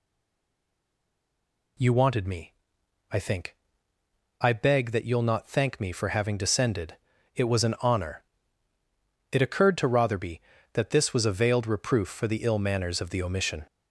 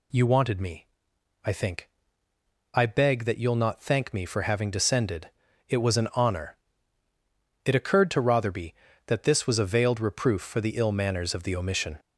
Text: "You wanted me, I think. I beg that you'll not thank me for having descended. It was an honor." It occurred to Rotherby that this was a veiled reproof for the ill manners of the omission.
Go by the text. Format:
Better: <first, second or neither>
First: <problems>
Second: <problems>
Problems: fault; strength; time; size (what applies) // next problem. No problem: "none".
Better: second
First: stays silent before the first word; noticeable; until 1.7 s; 1.7 s long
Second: none